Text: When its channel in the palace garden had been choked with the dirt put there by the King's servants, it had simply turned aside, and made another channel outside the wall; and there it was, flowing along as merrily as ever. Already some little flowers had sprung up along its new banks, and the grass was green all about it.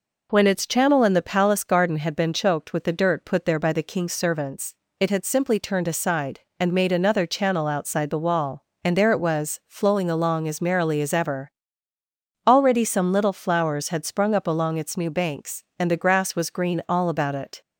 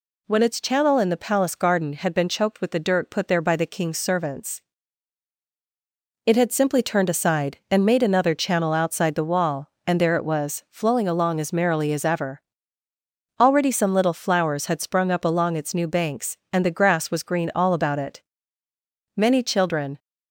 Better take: first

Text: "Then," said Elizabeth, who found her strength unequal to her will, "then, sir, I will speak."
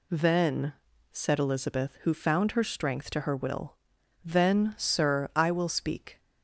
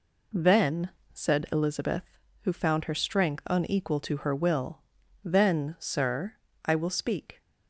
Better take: second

